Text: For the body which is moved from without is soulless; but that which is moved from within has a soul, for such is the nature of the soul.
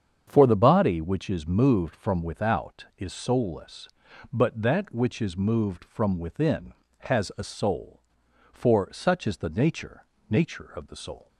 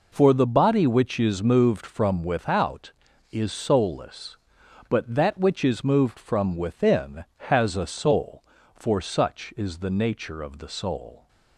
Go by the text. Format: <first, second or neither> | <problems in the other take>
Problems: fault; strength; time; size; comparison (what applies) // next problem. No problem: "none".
second | starts louder than the rest; strong; until 1.2 s; 7.5 dB // says "nature" twice; at 10.2 s